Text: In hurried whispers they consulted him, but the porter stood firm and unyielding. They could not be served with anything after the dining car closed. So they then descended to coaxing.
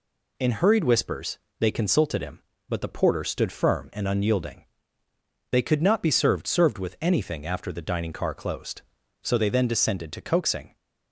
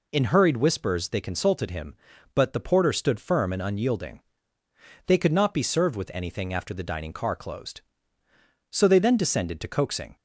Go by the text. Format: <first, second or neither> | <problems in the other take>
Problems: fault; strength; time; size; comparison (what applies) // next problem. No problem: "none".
second | pauses between "whispers" and "they"; slight; at 1.3 s; 0.22 s long // says "served" twice; at 6.4 s